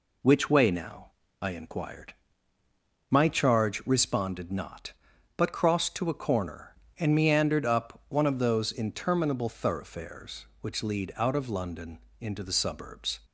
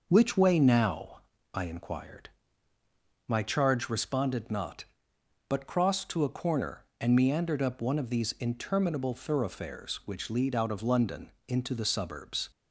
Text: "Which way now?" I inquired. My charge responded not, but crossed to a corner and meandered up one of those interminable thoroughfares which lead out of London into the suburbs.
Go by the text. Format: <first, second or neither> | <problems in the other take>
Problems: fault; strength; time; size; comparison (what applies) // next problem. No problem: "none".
first | says "these" for "those"; at 8.0 s // pauses between "London" and "into"; slight; at 11.3 s; 0.16 s long; slight in the first